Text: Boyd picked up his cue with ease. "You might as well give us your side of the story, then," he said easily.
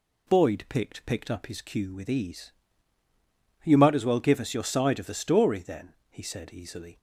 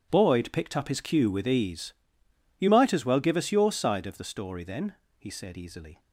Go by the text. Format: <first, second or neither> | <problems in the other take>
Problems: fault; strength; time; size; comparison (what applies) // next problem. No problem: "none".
second | says "picked" twice; at 1.0 s